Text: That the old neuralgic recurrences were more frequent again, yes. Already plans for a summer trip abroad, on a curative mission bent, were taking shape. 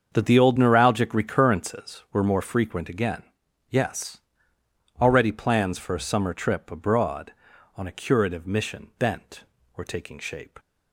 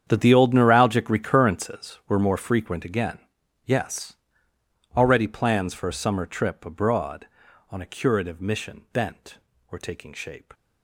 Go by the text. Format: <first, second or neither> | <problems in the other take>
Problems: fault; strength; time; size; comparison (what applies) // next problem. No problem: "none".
first | gets quieter; strong; throughout; 16.5 dB // starts louder than the rest; strong; until 1.0 s; 8.5 dB; also in the first